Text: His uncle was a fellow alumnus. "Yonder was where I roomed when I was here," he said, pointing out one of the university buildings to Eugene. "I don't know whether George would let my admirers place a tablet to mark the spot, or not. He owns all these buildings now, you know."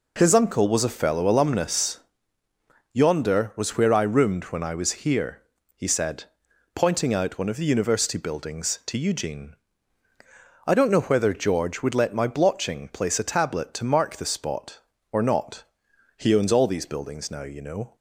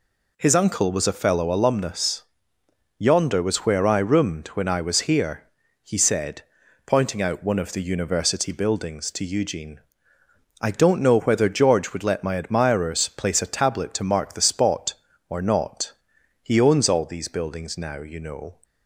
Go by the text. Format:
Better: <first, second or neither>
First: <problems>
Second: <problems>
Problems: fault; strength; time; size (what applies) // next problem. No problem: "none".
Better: second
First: says "blotching" for "admirers"; at 12.2 s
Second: none